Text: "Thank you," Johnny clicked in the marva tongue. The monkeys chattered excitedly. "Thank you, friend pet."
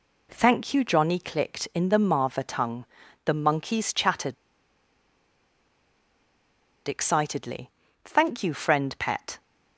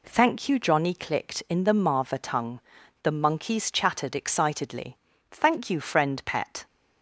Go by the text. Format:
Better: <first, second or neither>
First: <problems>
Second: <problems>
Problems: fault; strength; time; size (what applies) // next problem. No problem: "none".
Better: second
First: pauses between "chattered" and "excitedly"; strong; at 4.3 s; 2.5 s long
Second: none